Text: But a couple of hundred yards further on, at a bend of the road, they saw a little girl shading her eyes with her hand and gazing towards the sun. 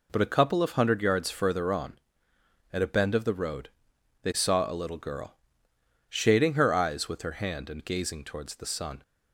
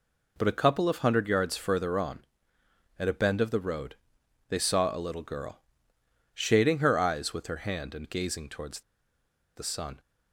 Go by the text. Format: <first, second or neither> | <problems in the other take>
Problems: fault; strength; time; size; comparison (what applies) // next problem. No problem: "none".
first | pauses between "girl" and "shading"; noticeable; at 5.6 s; 0.74 s long; noticeable in the first // pauses between "towards" and "the"; noticeable; at 8.8 s; 0.74 s long